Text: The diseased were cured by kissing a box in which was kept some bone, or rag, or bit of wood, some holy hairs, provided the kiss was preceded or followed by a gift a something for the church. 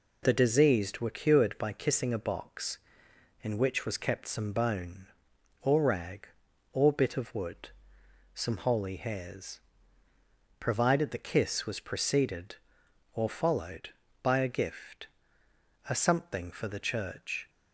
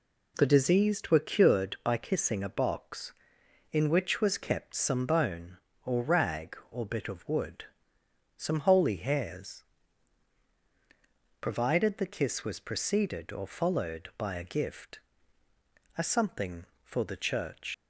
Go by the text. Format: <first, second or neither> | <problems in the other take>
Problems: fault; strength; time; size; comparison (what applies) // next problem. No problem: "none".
first | pauses between "gift" and "a"; noticeable; at 14.9 s; 0.98 s long; noticeable in the first // leaves "church" unfinished; at 17.7 s; 100 ms